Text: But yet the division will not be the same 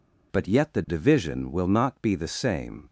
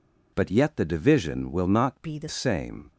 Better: first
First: none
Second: changes voice from "be" to "the"; from 2.0 to 2.2 s; 0.2 s long

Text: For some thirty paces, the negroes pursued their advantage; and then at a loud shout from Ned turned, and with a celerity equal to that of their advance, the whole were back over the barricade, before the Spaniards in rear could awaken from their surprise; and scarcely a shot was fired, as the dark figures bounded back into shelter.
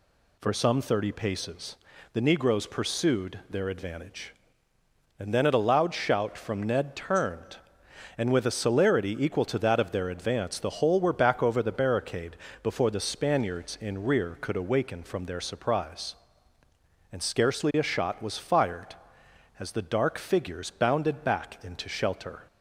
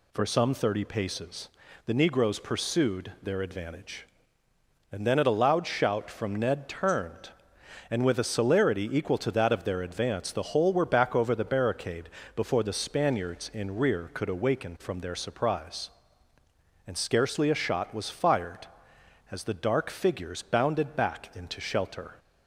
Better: neither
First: none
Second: none

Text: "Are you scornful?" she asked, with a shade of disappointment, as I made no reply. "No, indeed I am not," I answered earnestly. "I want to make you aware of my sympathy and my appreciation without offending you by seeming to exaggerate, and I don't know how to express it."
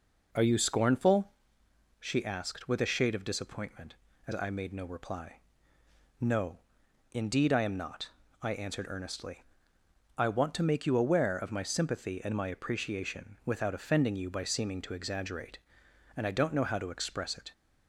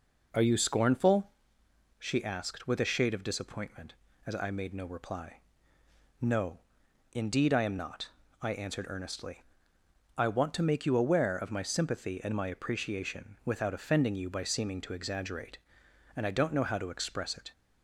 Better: neither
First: none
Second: none

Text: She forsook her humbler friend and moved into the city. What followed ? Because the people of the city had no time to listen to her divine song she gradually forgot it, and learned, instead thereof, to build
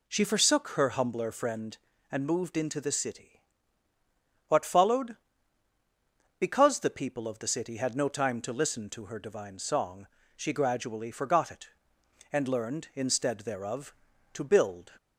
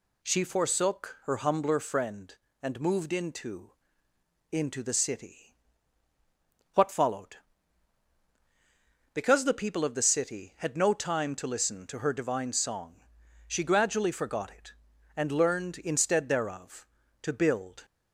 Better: first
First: pauses between "song" and "she"; slight; at 10.0 s; 0.32 s long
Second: says "into" twice; at 4.5 s // pauses between "song" and "she"; noticeable; at 12.9 s; 0.50 s long

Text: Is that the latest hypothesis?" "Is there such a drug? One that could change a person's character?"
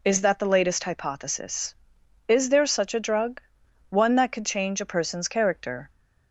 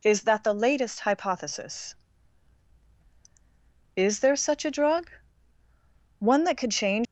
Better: first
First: none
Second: stops before "a person's character"; at 7.0 s

